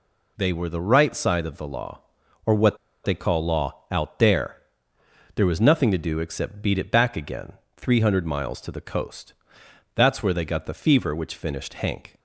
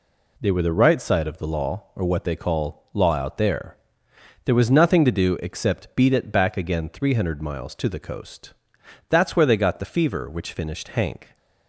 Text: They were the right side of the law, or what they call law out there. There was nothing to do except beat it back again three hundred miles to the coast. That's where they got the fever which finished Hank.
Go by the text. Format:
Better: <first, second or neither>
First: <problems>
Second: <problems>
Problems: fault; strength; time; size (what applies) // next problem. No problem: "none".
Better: second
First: pauses between "what" and "they"; slight; at 2.7 s; 0.27 s long // pauses between "again" and "three"; slight; at 7.5 s; 0.24 s long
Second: none